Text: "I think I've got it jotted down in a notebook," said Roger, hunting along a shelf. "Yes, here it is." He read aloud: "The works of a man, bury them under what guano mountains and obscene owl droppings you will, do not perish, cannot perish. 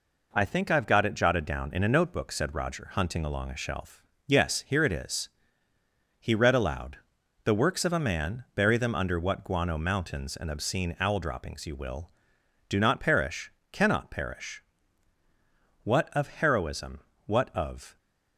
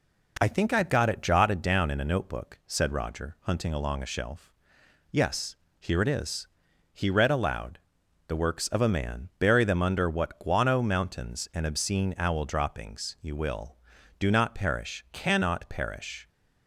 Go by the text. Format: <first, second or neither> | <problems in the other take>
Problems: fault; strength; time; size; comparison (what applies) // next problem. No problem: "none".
second | goes on to say "What of Heroism what of"; strong; from 15.8 s on; 2.1 s long